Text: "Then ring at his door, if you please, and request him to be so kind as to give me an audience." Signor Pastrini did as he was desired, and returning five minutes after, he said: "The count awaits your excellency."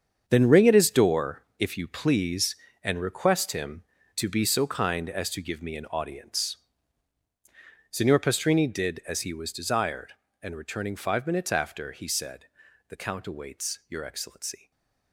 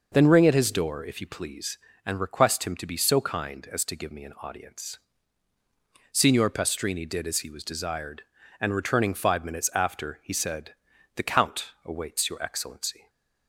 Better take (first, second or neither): second